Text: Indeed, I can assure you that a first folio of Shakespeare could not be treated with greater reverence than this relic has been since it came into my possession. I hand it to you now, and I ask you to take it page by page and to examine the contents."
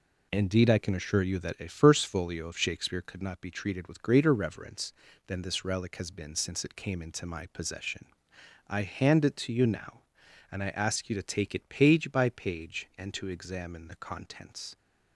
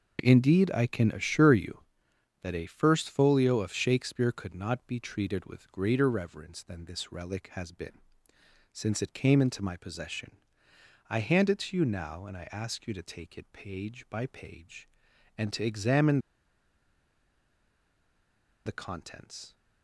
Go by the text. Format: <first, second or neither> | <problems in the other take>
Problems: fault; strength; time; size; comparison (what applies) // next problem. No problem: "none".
first | pauses between "been" and "since"; noticeable; at 7.9 s; 0.74 s long // pauses between "examine" and "the"; strong; at 16.1 s; 2.4 s long